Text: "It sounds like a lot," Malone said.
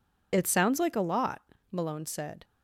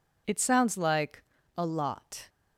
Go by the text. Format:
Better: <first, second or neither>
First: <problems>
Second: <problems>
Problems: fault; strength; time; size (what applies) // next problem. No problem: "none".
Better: first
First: none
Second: pauses between "like" and "a"; slight; at 1.2 s; 0.32 s long // stops before "Malone said"; at 2.2 s